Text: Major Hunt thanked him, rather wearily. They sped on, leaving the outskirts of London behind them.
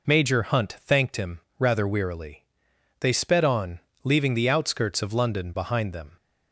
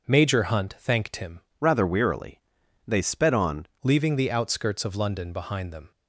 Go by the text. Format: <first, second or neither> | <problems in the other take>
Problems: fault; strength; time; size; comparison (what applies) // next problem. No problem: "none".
first | changes voice from "rather" to "on"; from 1.6 to 3.6 s; 2.0 s long